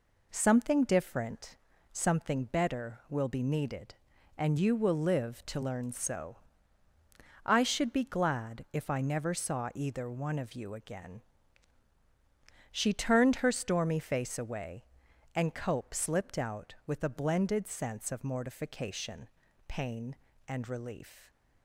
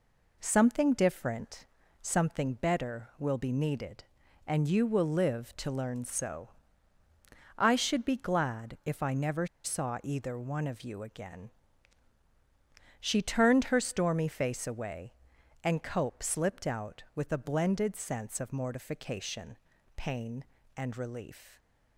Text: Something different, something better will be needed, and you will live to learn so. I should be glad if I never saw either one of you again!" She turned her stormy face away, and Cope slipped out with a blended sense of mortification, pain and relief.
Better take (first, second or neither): first